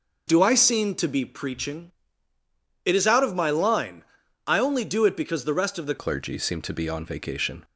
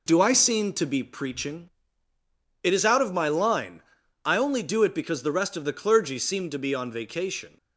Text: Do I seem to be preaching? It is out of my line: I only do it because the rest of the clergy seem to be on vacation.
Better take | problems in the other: second | changes voice at "clergy"; from 5.9 s on; 1.7 s long

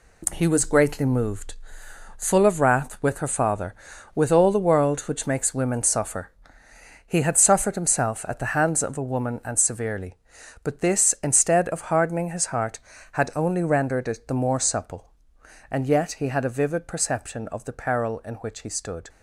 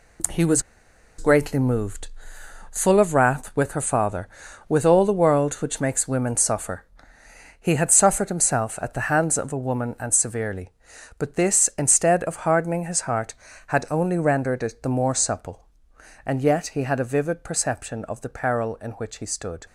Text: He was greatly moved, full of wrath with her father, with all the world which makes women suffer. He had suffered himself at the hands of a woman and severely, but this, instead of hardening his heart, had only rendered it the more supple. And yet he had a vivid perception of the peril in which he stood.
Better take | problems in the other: first | pauses between "was" and "greatly"; noticeable; at 0.6 s; 0.57 s long

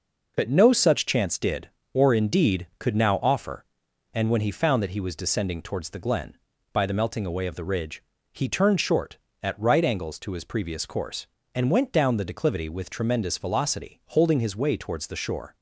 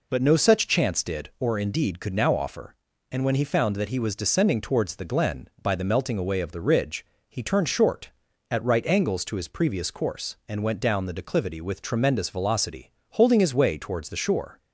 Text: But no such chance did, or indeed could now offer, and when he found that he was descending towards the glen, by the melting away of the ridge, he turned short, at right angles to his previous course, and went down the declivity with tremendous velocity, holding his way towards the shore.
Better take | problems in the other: neither | none

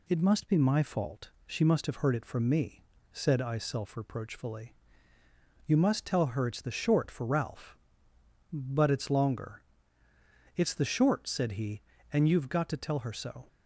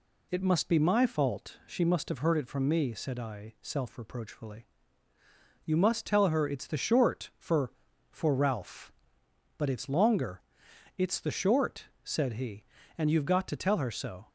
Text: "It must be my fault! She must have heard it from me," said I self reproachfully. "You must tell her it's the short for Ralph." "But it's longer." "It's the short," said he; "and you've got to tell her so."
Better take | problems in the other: first | says "for" twice; at 8.1 s

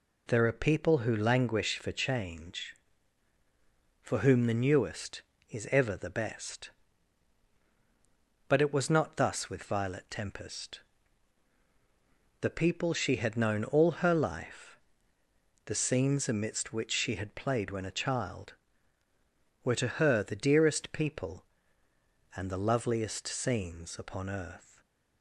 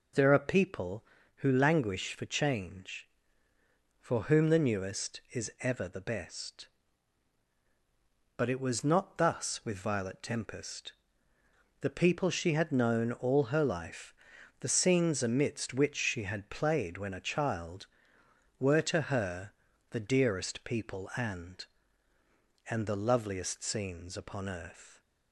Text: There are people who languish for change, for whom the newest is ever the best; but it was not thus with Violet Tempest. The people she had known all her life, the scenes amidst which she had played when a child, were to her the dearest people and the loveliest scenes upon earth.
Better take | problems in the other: first | pauses between "her" and "the"; at 19.5 s; 0.40 s long // says "and" twice; at 22.7 s

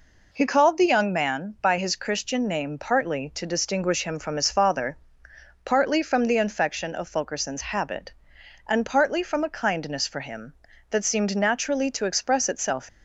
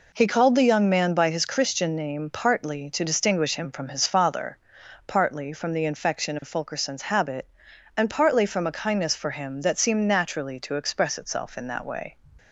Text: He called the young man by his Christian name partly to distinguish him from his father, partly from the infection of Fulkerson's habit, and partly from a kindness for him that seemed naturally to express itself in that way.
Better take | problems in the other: second | stops before "in that way"; at 12.8 s

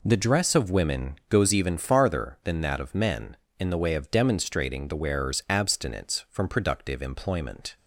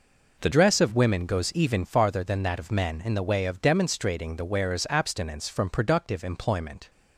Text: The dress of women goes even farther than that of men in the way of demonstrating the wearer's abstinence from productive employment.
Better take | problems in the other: first | changes voice at "dress"; from 0.5 s on; 6.3 s long

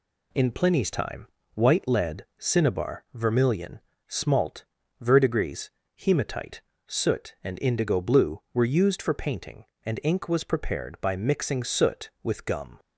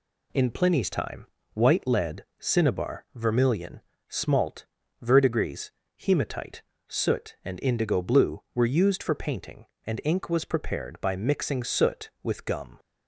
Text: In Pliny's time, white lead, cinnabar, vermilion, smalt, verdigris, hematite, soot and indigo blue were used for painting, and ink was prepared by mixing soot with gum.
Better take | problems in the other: neither | none

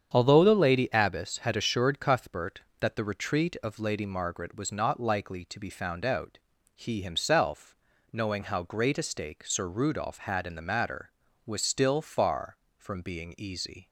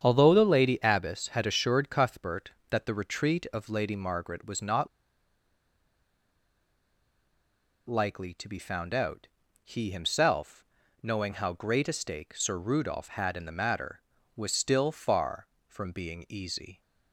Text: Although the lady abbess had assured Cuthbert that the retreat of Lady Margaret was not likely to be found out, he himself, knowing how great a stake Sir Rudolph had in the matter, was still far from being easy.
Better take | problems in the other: first | starts louder than the rest; strong; until 1.0 s; 8 dB; strong in the first // pauses between "not" and "likely"; strong; at 4.8 s; 3.0 s long

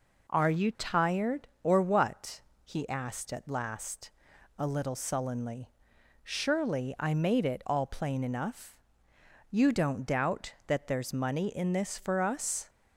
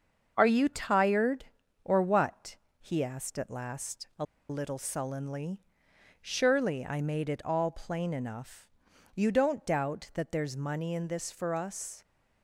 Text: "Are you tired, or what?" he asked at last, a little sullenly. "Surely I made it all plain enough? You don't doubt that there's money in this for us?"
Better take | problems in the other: first | starts louder than the rest; until 1.3 s; 6.5 dB // pauses between "a" and "little"; slight; at 4.2 s; 0.24 s long

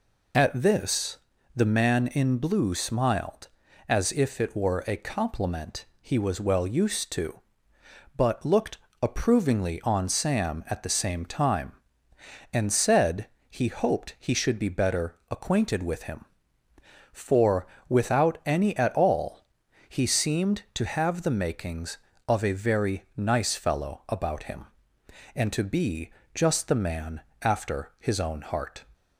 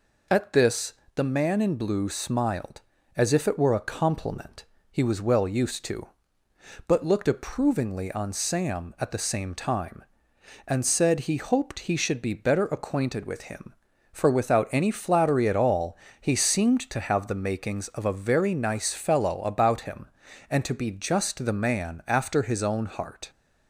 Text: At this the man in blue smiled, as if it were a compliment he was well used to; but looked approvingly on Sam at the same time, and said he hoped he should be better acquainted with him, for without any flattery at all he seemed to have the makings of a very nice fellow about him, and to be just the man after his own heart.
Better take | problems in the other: second | pauses between "this" and "the"; at 1.1 s; 0.40 s long; slight in the second // pauses between "compliment" and "he"; slight; at 5.8 s; 0.16 s long; slight in the second // pauses between "looked" and "approvingly"; slight; at 8.7 s; 0.26 s long // pauses between "said" and "he"; slight; at 13.2 s; 0.22 s long // pauses between "for" and "without"; slight; at 17.6 s; 0.22 s long // skips "flattery"; at 18.7 s // pauses between "all" and "he"; at 19.4 s; 0.42 s long; slight in the second // pauses between "be" and "just"; slight; at 26.0 s; 0.24 s long // pauses between "man" and "after"; slight; at 27.2 s; 0.18 s long

